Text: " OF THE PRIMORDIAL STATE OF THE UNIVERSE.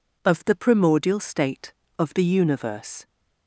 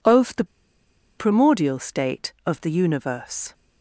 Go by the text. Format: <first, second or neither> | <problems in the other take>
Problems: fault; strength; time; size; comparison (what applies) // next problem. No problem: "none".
first | pauses between "THE" and "PRIMORDIAL"; noticeable; at 0.4 s; 0.73 s long